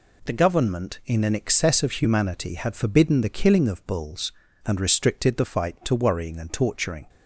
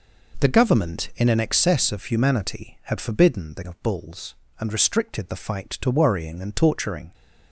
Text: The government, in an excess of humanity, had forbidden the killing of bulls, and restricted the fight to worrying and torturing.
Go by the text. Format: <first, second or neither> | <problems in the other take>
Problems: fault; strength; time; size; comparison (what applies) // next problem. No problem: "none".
first | skips "killing"; at 3.6 s